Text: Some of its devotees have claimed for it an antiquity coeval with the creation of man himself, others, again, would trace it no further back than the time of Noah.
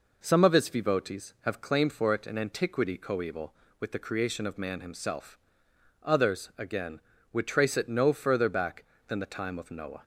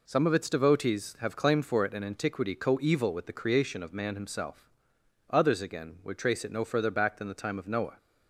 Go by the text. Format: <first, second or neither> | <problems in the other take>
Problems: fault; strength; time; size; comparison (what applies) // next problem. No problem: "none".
neither | none